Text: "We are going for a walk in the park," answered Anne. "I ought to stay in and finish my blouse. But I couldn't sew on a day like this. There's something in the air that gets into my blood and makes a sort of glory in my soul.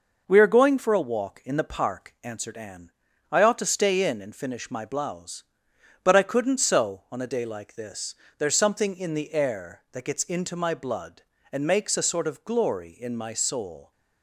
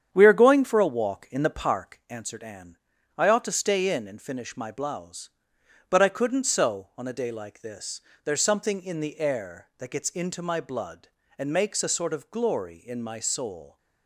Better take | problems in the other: first | starts louder than the rest; strong; until 2.0 s; 8.5 dB

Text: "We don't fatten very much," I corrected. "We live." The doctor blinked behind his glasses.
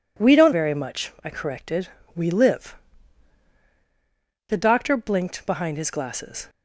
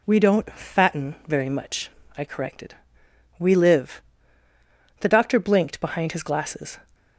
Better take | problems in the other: second | skips "fatten"; at 0.5 s

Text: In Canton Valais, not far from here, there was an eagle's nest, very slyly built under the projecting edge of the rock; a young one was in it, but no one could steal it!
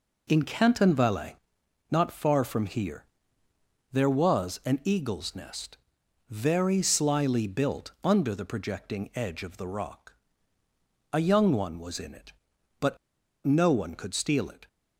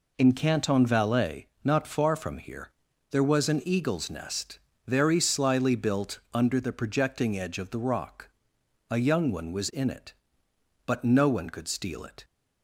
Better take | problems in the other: second | pauses between "but" and "no"; noticeable; at 12.9 s; 0.48 s long

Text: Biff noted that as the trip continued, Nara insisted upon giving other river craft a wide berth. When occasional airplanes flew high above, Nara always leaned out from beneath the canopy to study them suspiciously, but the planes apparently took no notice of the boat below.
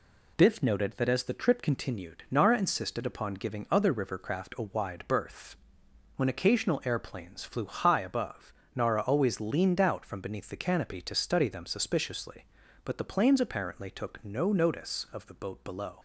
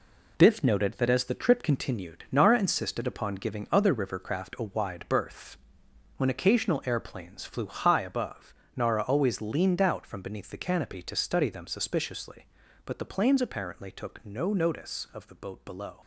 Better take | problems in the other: first | gets quieter; strong; throughout; 7.5 dB

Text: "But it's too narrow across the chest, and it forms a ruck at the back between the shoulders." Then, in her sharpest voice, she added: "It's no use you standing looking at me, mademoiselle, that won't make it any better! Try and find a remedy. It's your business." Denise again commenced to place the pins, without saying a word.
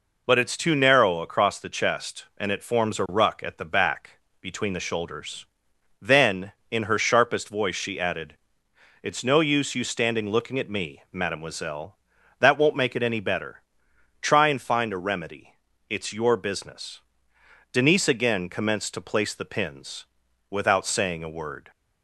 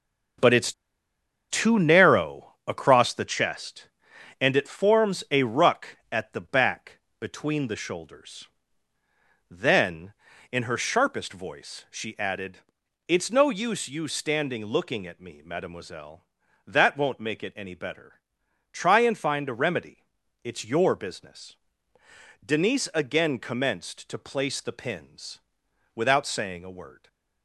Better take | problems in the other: first | starts louder than the rest; until 2.2 s; 6.5 dB // pauses between "it's" and "too"; noticeable; at 0.7 s; 0.79 s long // pauses between "back" and "between"; slight; at 6.9 s; 0.20 s long; slight in the first // stays silent after the last word; slight; from 26.9 s on; 0.5 s long

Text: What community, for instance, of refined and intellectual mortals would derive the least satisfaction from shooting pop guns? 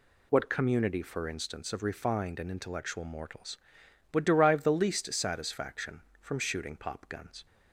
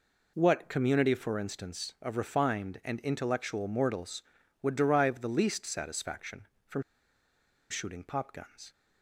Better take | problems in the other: first | pauses between "from" and "shooting"; noticeable; at 6.8 s; 0.87 s long

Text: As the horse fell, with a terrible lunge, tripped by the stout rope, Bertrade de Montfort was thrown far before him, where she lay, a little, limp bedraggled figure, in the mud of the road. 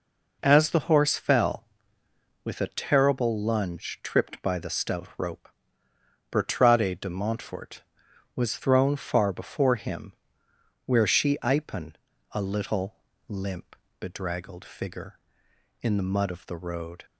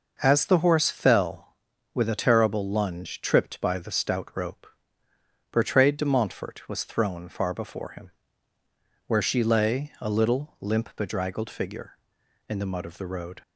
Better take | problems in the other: second | says "ipen" for "lay"; at 11.4 s // pauses between "limp" and "bedraggled"; slight; at 13.7 s; 0.24 s long

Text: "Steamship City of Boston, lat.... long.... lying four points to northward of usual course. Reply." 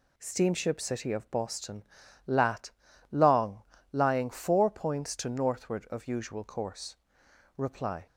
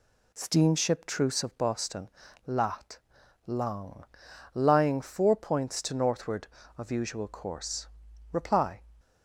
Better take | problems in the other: first | says "Truce" for "City"; at 1.0 s

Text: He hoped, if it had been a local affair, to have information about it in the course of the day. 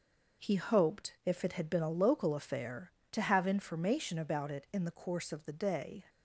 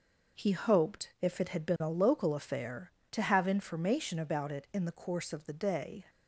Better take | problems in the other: neither | none

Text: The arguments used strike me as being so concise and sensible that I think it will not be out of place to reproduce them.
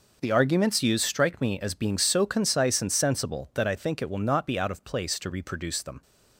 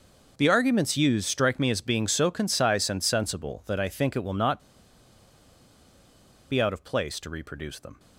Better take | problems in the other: first | pauses between "not" and "be"; strong; at 4.5 s; 1.9 s long

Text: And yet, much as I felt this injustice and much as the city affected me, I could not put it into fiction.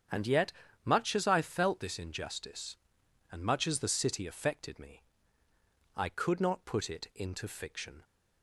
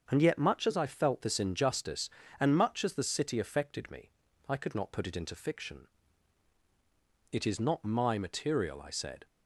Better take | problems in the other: first | starts louder than the rest; until 1.1 s; 7 dB; strong in the first // goes on to say "It is not my material I said"; strong; from 7.3 s on; 1.9 s long

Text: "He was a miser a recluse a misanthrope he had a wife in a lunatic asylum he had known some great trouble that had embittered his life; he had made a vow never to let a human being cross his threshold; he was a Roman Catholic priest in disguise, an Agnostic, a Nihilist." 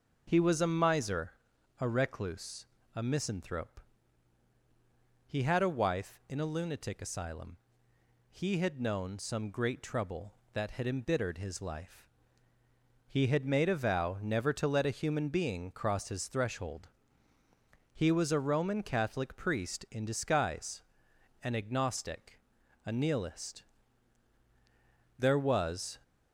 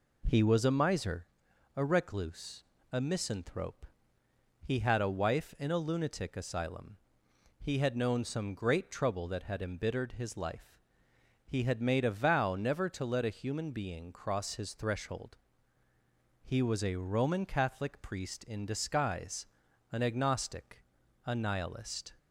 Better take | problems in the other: second | pauses between "miser" and "a"; noticeable; at 1.3 s; 0.50 s long; noticeable in the second // pauses between "recluse" and "a"; slight; at 2.6 s; 0.28 s long; slight in the second // pauses between "misanthrope" and "he"; strong; at 3.8 s; 1.4 s long; noticeable in the second // pauses between "asylum" and "he"; noticeable; at 7.5 s; 0.74 s long; noticeable in the second // goes on to say "There was"; noticeable; from 25.1 s on; 0.78 s long

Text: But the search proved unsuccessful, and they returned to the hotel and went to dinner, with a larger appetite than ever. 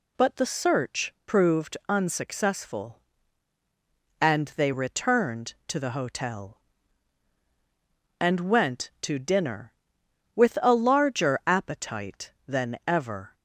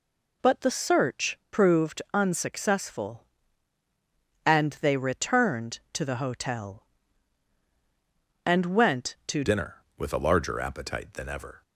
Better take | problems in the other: first | changes voice at "dinner"; from 9.4 s on; 2.2 s long

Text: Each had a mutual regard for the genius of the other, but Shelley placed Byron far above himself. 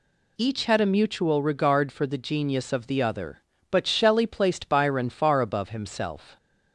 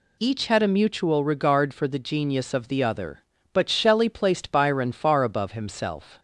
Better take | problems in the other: neither | none

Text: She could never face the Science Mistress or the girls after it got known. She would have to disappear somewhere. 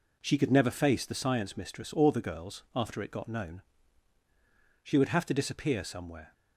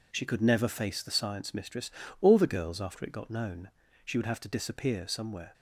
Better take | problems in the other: neither | none

